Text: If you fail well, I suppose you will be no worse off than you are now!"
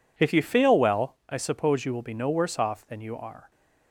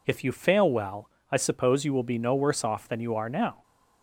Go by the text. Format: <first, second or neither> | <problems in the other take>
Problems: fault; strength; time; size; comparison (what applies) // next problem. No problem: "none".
second | stops before "now"; at 3.5 s